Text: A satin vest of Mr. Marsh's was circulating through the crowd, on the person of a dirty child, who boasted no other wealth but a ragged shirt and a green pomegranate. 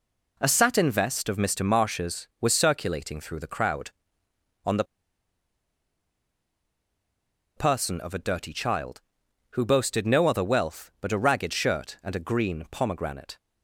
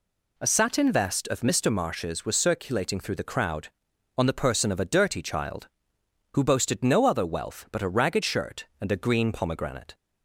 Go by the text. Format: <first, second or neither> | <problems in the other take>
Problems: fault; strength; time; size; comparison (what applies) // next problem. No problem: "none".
second | pauses between "the" and "person"; strong; at 4.8 s; 2.7 s long